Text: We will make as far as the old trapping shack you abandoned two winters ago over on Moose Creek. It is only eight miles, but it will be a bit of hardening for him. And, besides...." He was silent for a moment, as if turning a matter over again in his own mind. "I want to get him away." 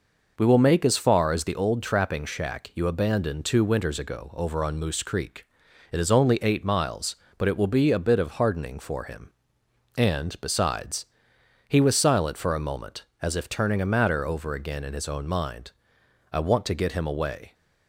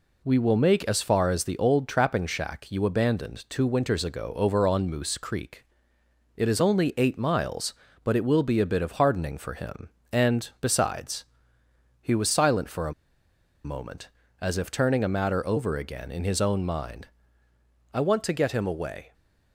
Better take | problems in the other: first | pauses between "a" and "moment"; noticeable; at 12.9 s; 0.72 s long

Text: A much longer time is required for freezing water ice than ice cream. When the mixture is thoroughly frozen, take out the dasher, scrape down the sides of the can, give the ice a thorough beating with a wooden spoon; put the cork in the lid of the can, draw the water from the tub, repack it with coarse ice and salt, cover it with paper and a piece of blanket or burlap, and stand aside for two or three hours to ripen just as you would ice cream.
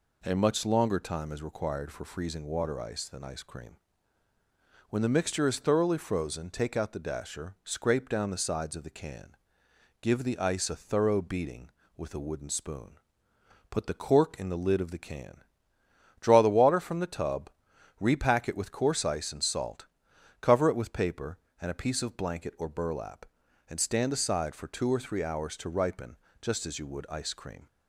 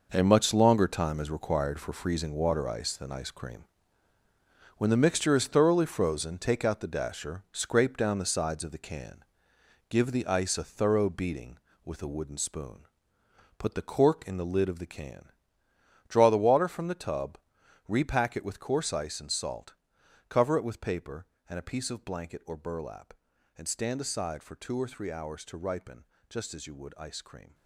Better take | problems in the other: first | gets quieter; strong; throughout; 10.5 dB // pauses between "ripen" and "just"; slight; at 26.0 s; 0.26 s long; slight in the first

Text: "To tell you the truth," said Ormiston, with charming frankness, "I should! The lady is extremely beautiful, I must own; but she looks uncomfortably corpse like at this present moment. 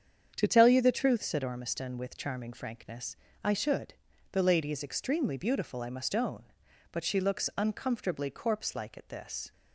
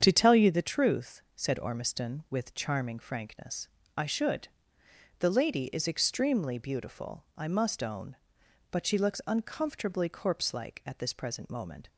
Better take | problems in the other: second | starts louder than the rest; strong; until 1.3 s; 7.5 dB; strong in the second // stops before "present moment"; at 9.5 s

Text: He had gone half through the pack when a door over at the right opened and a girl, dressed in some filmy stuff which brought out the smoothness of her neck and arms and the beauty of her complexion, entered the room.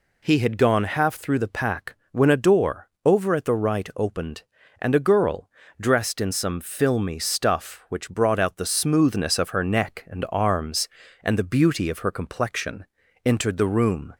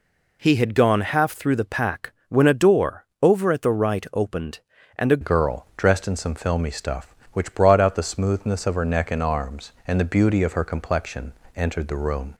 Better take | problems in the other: first | pauses between "pack" and "when"; slight; at 2.1 s; 0.18 s long; slight in the first // pauses between "door" and "over"; slight; at 3.0 s; 0.16 s long; slight in the first // changes voice at "girl"; from 5.2 s on; 7.1 s long

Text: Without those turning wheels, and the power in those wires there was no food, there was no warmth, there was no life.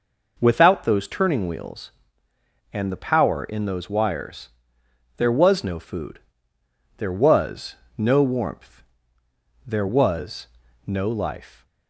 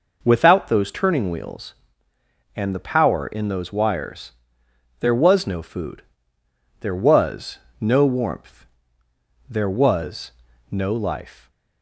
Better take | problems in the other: neither | pauses between "wires" and "there"; noticeable; the same in both // pauses between "was" and "no"; slight; the same in both // pauses between "was" and "no"; the same in both

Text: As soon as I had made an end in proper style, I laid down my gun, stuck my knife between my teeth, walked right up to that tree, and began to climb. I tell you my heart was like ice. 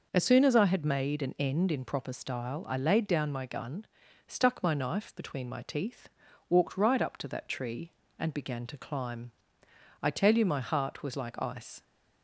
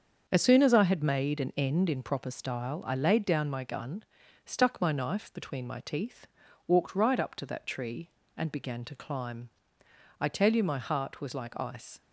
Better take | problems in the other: first | gets quieter; strong; throughout; 7.5 dB

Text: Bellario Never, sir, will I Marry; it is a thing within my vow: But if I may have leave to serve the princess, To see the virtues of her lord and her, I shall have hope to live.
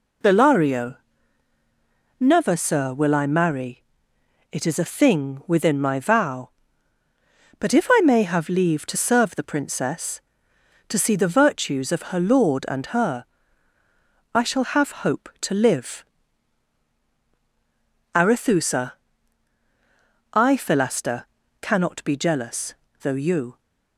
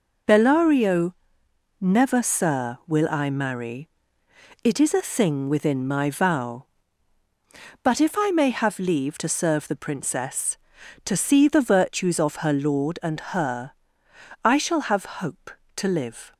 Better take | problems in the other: second | pauses between "Bellario" and "Never"; at 0.9 s; 1.2 s long; noticeable in the second // goes on to say "Arethusa I Philaster Cannot be jealous though you"; strong; from 18.1 s on; 5.4 s long

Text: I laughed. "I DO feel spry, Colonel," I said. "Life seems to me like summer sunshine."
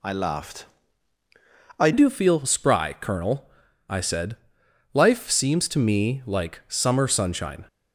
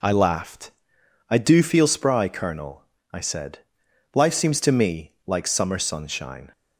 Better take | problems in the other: second | changes voice at "DO"; from 1.9 s on; 5.7 s long

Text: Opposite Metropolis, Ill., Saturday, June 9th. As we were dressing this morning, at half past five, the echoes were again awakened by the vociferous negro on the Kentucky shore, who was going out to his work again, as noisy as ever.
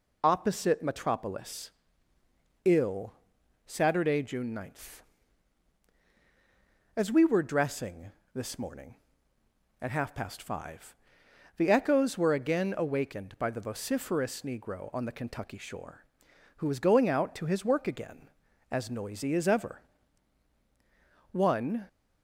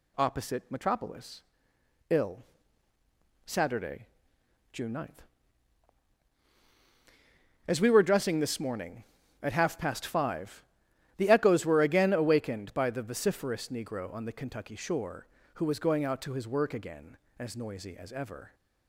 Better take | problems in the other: second | pauses between "dressing" and "this"; slight; at 8.1 s; 0.24 s long // goes on to say "One"; from 21.3 s on; 0.54 s long

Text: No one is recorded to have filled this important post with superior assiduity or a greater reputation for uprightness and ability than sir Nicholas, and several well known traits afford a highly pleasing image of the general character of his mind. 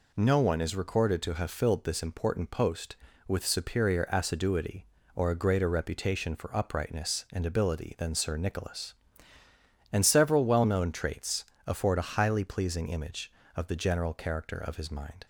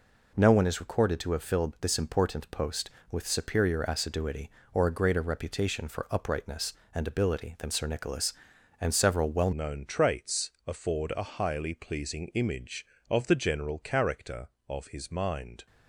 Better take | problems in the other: first | changes voice at "known"; from 9.5 s on; 6.1 s long // pauses between "traits" and "afford"; slight; at 10.4 s; 0.16 s long; slight in the first

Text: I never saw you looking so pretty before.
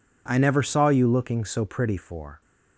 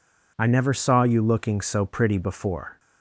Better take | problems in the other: second | says "for" for "before"; at 1.9 s

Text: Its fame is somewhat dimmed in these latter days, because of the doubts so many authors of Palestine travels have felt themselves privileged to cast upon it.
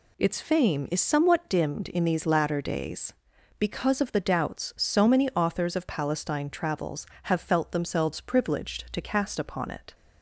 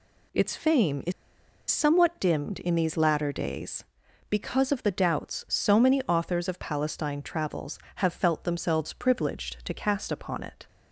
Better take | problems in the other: first | pauses between "is" and "somewhat"; noticeable; at 1.1 s; 0.58 s long

